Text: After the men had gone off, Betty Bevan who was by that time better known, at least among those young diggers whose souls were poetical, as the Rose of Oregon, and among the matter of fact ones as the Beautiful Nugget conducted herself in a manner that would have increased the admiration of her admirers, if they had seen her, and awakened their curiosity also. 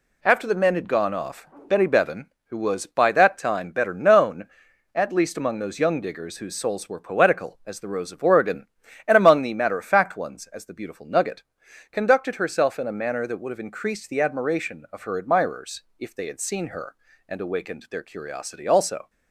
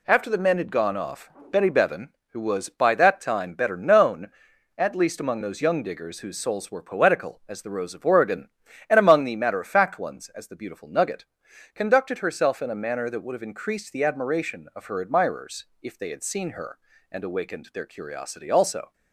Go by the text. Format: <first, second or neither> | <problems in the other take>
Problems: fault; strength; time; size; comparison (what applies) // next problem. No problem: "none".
neither | pauses between "Nugget" and "conducted"; noticeable; the same in both